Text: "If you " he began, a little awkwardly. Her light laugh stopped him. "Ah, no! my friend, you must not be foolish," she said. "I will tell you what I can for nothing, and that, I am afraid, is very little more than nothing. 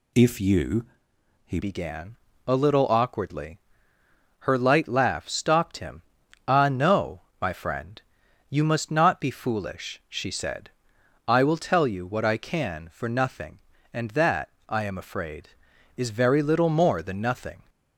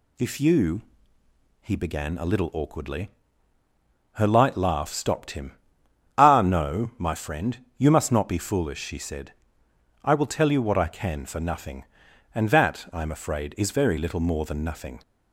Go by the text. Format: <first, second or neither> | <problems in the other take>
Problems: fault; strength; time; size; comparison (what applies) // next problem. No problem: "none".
second | changes voice at "began"; from 1.5 s on; 16.1 s long